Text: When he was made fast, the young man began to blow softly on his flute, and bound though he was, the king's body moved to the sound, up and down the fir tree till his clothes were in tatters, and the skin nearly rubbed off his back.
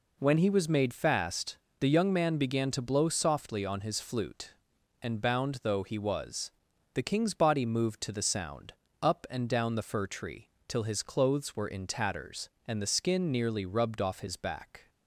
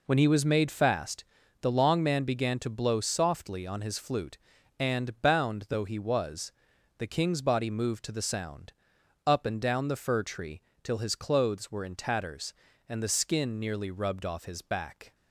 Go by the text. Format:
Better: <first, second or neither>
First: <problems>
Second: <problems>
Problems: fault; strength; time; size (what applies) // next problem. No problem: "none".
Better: first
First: pauses between "tree" and "till"; slight; at 10.4 s; 0.18 s long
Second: says "long" for "young"; at 1.7 s // pauses between "tree" and "till"; slight; at 10.6 s; 0.22 s long